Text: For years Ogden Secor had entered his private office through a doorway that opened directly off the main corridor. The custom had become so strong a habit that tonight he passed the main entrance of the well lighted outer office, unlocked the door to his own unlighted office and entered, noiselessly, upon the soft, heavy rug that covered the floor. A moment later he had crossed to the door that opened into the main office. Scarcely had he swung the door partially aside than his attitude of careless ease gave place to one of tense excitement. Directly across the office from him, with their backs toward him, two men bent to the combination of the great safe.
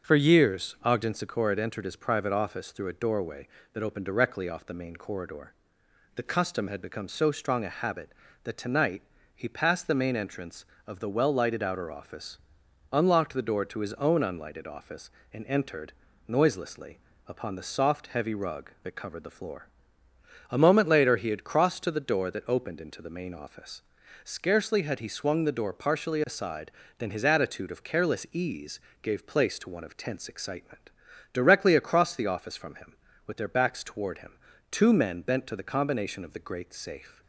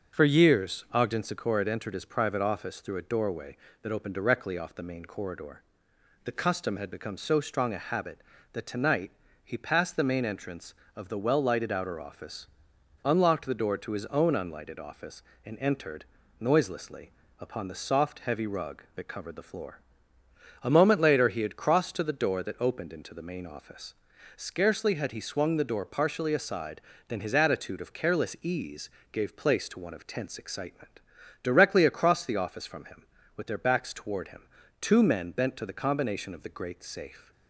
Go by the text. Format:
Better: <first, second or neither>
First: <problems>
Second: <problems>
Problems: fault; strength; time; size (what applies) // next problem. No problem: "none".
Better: neither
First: starts louder than the rest; until 1.1 s; 7 dB // pauses between "tonight" and "he"; slight; at 9.0 s; 0.34 s long // pauses between "ease" and "gave"; slight; at 28.7 s; 0.22 s long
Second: starts louder than the rest; until 1.2 s; 7 dB // pauses between "tonight" and "he"; slight; at 9.1 s; 0.34 s long // pauses between "ease" and "gave"; slight; at 28.8 s; 0.22 s long